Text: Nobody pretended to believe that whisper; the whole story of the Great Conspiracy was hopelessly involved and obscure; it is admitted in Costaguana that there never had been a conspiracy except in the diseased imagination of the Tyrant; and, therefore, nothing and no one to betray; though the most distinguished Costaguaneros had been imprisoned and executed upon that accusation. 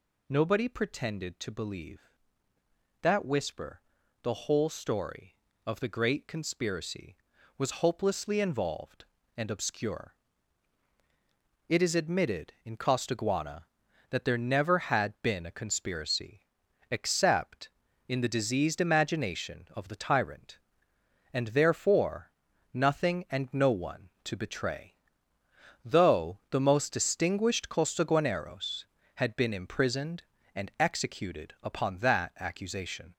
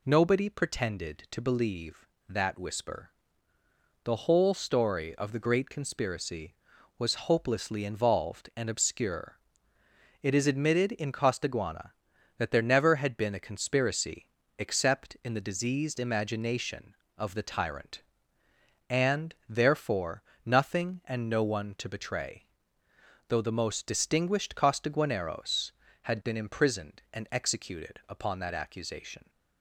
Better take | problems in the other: second | gets louder; throughout; 3.5 dB // pauses between "conspiracy" and "except"; noticeable; at 16.4 s; 0.46 s long; slight in the second

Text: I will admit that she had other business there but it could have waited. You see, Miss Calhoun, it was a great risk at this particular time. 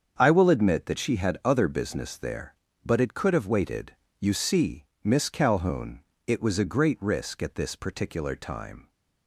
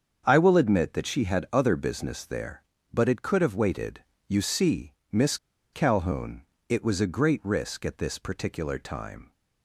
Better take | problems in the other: first | starts louder than the rest; until 1.2 s; 7 dB; also in the first // pauses between "Miss" and "Calhoun"; at 5.3 s; 0.36 s long

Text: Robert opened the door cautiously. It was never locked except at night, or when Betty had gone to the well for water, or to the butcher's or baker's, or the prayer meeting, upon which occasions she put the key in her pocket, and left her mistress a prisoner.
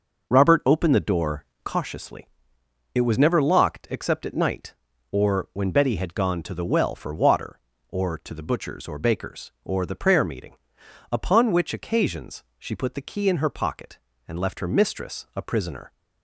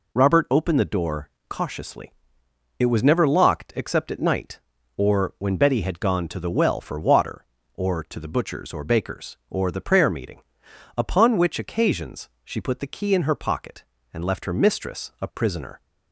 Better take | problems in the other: second | starts louder than the rest; noticeable; until 1.9 s; 6 dB // pauses between "door" and "cautiously"; slight; at 1.4 s; 0.18 s long; slight in the second // pauses between "occasions" and "she"; slight; at 12.4 s; 0.16 s long; slight in the second

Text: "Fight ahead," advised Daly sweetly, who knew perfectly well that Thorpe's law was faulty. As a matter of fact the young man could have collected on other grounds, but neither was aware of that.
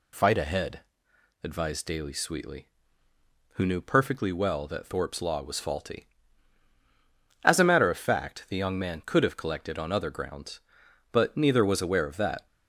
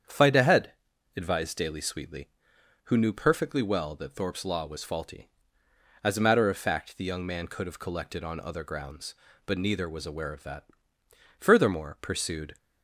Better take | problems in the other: first | starts louder than the rest; strong; until 1.4 s; 8 dB // goes on to say "Furthermore pursued"; noticeable; from 11.3 s on; 1.1 s long

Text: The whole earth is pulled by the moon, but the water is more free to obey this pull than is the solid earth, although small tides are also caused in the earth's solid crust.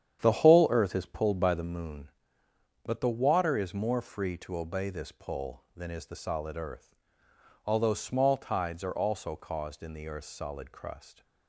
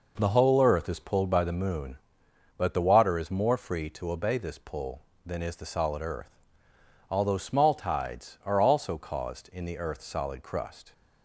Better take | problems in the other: second | starts louder than the rest; strong; until 1.7 s; 9 dB

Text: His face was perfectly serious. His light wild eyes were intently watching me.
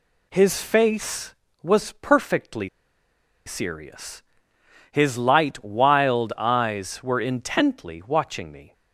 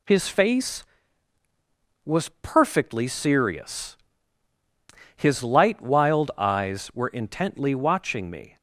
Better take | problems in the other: second | pauses between "perfectly" and "serious"; noticeable; at 2.6 s; 0.77 s long

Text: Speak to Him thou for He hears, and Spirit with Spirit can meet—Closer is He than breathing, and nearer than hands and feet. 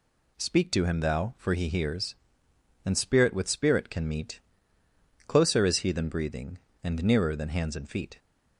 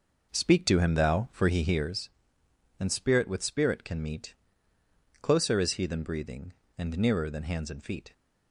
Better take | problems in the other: first | starts louder than the rest; noticeable; until 2.0 s; 5.5 dB

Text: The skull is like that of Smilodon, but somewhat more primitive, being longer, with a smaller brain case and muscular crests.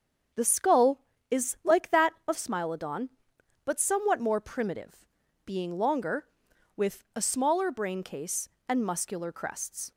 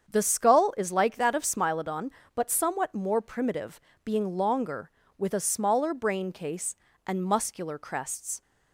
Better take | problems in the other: neither | starts louder than the rest; strong; the same in both

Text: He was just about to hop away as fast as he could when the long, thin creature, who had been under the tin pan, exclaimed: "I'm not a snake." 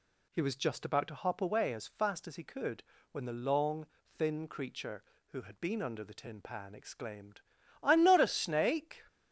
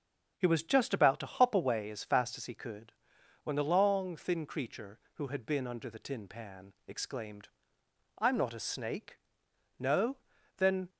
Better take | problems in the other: first | starts louder than the rest; until 1.3 s; 6.5 dB // pauses between "could" and "when"; noticeable; at 2.9 s; 0.52 s long; slight in the first // goes on to say "No Then"; noticeable; from 9.7 s on; 1.1 s long

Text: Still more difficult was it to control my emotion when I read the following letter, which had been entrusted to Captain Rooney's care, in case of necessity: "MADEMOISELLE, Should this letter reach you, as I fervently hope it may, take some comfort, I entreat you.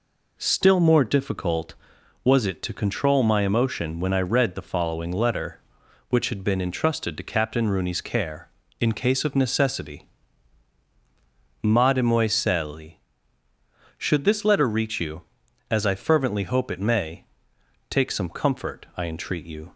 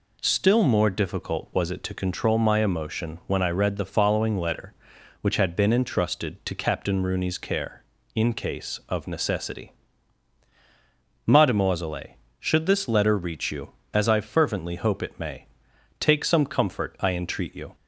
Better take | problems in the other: neither | none

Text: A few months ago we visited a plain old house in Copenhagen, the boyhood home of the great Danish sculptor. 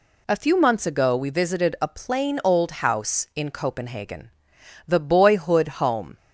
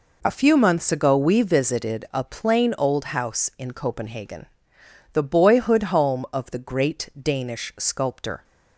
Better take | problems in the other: second | stops before "of the great Danish sculptor"; at 6.1 s

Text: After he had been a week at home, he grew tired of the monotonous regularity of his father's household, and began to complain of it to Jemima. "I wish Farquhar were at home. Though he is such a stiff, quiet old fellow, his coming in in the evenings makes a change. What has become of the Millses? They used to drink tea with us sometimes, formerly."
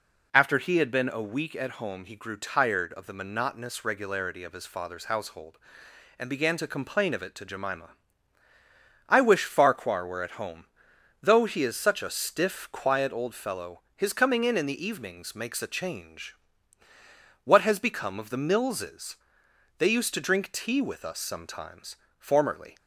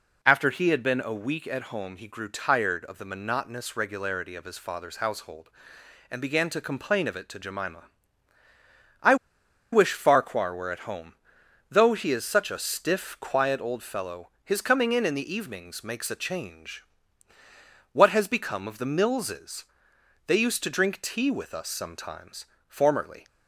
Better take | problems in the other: first | pauses between "I" and "wish"; noticeable; at 9.1 s; 0.56 s long

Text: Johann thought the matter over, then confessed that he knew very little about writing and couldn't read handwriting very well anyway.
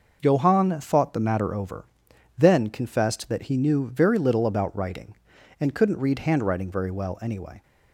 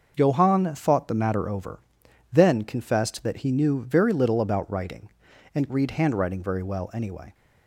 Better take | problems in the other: first | starts louder than the rest; noticeable; until 1.1 s; 6 dB // skips "couldn't"; at 5.7 s

